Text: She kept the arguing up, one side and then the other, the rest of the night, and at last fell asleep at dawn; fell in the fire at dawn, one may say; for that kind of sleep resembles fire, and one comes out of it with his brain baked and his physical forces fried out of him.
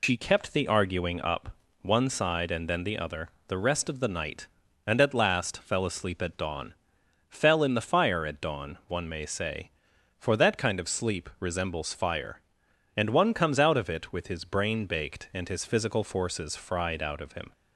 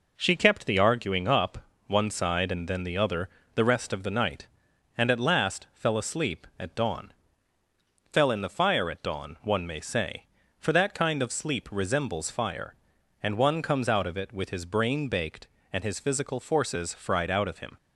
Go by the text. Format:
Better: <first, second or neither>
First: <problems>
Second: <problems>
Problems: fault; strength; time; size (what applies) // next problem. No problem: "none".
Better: second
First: loses the start of "She"; at 0.0 s; 80 ms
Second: none